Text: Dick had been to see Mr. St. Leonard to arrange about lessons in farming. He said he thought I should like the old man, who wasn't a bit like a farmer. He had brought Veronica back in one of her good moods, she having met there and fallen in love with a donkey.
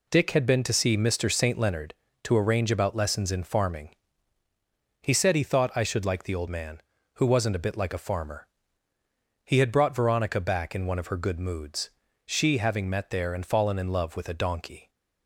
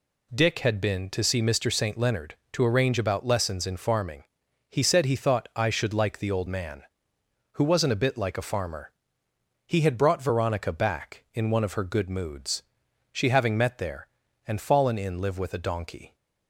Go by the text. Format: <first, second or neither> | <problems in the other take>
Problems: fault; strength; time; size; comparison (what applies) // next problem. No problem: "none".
first | says "live" for "love"; at 15.2 s